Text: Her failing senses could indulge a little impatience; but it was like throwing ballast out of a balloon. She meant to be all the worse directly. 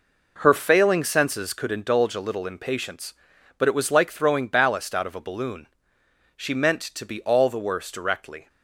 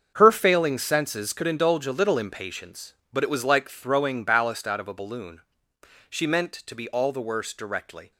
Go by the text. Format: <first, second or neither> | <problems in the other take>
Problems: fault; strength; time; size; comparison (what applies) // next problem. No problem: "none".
first | gets quieter; strong; throughout; 12 dB